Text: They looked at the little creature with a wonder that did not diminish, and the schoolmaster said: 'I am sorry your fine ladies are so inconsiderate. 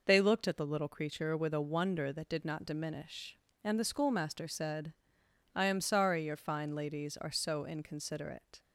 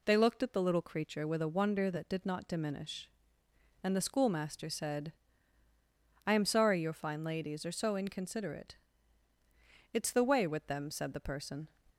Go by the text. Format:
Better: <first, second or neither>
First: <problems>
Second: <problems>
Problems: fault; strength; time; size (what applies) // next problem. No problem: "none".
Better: first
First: none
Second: goes on to say "It's the way with them said the person"; strong; from 9.9 s on; 1.7 s long